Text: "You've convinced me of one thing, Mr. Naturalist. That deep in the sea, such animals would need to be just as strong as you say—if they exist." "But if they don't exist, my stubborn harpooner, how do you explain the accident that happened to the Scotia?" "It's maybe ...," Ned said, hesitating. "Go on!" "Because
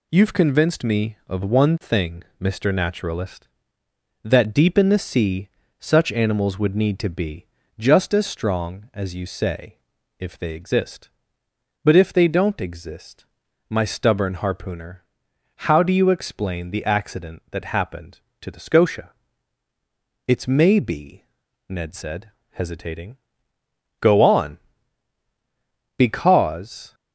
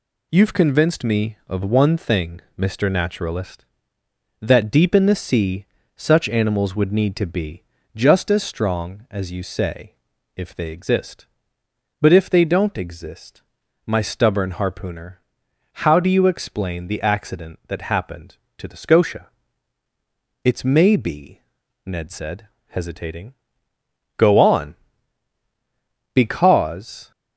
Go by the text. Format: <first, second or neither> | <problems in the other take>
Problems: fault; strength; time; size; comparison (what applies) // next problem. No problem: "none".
neither | pauses between "be" and "just"; slight; the same in both